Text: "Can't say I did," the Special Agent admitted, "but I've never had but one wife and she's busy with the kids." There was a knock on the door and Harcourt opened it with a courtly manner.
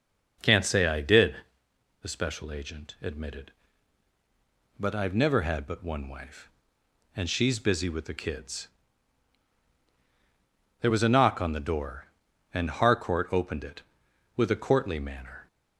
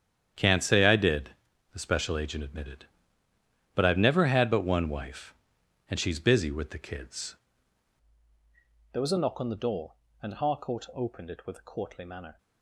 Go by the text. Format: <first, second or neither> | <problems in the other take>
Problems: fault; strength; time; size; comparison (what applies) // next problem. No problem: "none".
first | starts louder than the rest; strong; until 1.7 s; 9.5 dB // changes voice at "There"; from 8.9 s on; 3.4 s long